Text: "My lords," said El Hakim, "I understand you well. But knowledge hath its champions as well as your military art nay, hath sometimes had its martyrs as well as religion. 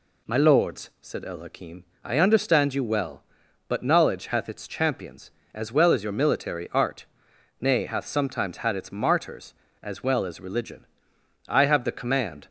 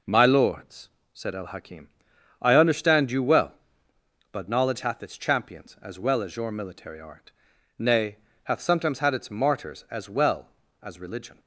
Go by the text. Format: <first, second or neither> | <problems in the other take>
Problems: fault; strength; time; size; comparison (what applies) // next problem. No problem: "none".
second | pauses between "art" and "nay"; noticeable; at 7.0 s; 0.56 s long; noticeable in the second // goes on to say "I have the command"; noticeable; from 11.4 s on; 1.0 s long